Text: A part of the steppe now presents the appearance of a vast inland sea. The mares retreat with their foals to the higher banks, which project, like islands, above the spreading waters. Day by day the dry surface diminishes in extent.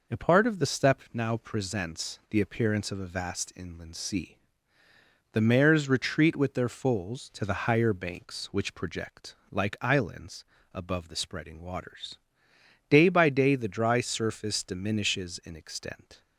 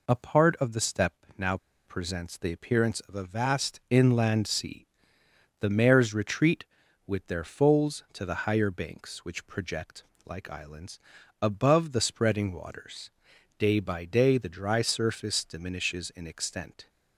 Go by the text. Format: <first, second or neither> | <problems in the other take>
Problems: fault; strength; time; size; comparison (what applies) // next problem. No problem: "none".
first | pauses between "now" and "presents"; slight; at 1.5 s; 0.29 s long